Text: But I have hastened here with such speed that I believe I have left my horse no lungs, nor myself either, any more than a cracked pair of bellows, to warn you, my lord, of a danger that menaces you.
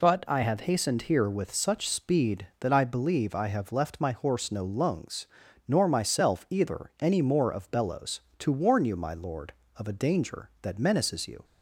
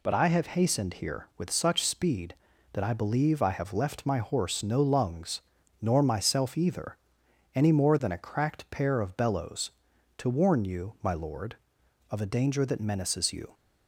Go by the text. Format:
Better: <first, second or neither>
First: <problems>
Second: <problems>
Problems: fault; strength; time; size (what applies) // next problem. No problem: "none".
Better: second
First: skips "than a cracked pair"; at 7.5 s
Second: none